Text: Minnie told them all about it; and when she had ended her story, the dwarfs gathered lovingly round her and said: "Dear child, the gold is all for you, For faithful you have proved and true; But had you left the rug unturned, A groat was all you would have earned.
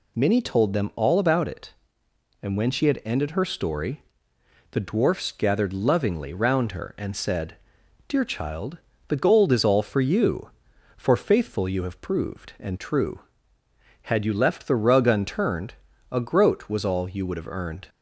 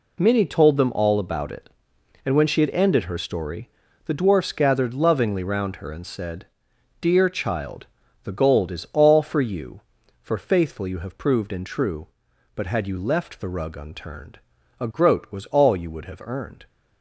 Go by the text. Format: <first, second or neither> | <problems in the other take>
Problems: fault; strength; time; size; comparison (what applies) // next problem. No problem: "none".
second | skips "But"; at 13.6 s